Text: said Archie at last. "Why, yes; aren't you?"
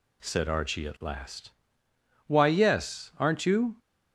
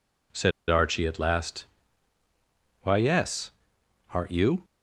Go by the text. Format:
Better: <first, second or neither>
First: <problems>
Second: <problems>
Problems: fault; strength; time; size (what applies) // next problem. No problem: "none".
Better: first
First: none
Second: pauses between "said" and "Archie"; slight; at 0.5 s; 0.19 s long